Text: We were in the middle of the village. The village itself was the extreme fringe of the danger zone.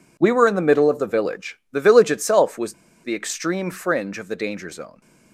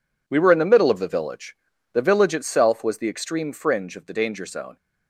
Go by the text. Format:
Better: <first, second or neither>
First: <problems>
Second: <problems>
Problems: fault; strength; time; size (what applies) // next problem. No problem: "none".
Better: second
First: pauses between "was" and "the"; slight; at 2.7 s; 0.30 s long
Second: none